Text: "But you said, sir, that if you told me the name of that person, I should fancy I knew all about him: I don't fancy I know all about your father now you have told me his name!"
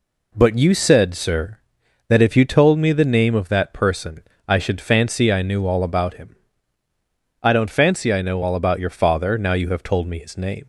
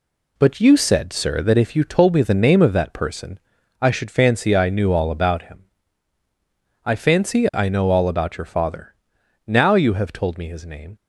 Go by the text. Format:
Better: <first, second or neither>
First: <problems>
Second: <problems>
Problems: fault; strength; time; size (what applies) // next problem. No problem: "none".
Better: first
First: none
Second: skips "don't"; at 6.9 s // pauses between "father" and "now"; noticeable; at 8.9 s; 0.52 s long